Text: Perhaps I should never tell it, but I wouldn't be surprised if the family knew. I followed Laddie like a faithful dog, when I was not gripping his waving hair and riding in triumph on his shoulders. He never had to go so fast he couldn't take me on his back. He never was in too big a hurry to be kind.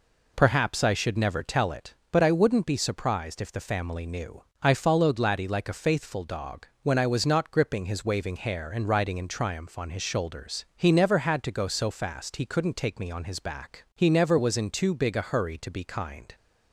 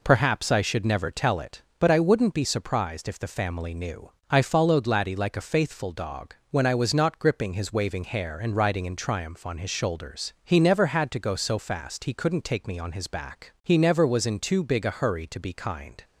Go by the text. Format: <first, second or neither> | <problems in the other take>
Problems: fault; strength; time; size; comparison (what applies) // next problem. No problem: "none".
neither | none